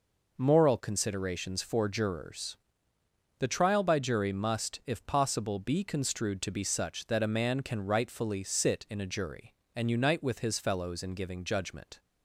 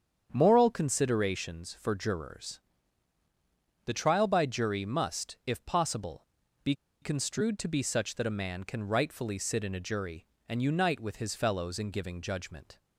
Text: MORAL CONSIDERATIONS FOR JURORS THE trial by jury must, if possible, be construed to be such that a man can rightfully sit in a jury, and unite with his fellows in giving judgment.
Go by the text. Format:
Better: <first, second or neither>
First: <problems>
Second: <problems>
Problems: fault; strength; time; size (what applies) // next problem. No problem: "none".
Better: first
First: pauses between "JURORS" and "THE"; noticeable; at 2.5 s; 0.82 s long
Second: starts louder than the rest; strong; until 1.3 s; 8 dB // pauses between "JURORS" and "THE"; at 2.6 s; 1.2 s long // pauses between "be" and "construed"; slight; at 6.7 s; 0.29 s long